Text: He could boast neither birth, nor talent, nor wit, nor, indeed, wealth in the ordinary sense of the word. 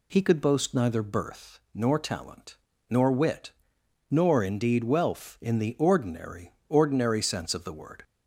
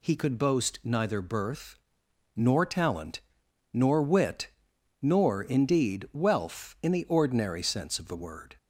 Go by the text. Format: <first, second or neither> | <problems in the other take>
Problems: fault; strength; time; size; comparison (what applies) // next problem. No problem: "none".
second | says "ordinary" twice; at 6.6 s